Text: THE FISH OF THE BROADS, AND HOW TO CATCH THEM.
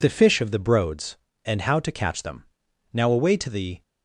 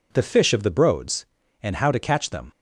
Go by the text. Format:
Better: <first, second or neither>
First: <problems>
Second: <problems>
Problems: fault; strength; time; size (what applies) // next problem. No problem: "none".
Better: second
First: goes on to say "Now away to the"; noticeable; from 2.9 s on; 0.90 s long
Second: none